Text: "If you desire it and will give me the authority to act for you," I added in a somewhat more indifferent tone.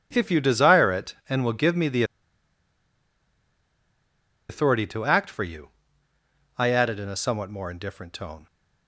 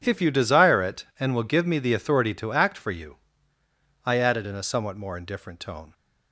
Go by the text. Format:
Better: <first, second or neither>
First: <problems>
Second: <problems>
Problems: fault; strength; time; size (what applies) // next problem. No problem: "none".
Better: second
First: pauses between "the" and "authority"; strong; at 2.0 s; 2.4 s long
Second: none